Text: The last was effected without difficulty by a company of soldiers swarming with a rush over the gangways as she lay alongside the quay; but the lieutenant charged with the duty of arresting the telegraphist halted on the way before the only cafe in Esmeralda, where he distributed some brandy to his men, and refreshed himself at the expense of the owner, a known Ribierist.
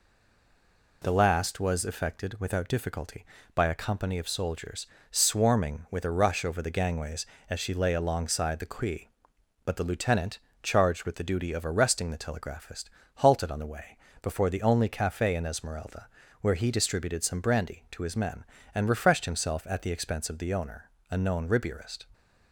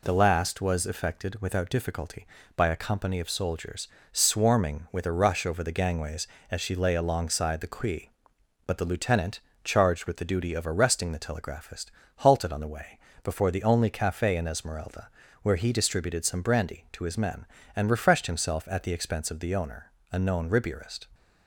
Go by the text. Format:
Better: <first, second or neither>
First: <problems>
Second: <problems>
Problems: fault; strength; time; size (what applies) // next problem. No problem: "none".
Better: second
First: stays silent before the first word; until 1.0 s; 1.0 s long // pauses between "soldiers" and "swarming"; slight; at 4.8 s; 0.24 s long // pauses between "lieutenant" and "charged"; slight; at 10.3 s; 0.24 s long // pauses between "telegraphist" and "halted"; slight; at 12.8 s; 0.26 s long // pauses between "way" and "before"; slight; at 13.9 s; 0.24 s long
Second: pauses between "soldiers" and "swarming"; slight; at 3.8 s; 0.24 s long // pauses between "lieutenant" and "charged"; slight; at 9.3 s; 0.24 s long // pauses between "telegraphist" and "halted"; slight; at 11.8 s; 0.26 s long // pauses between "way" and "before"; slight; at 12.9 s; 0.24 s long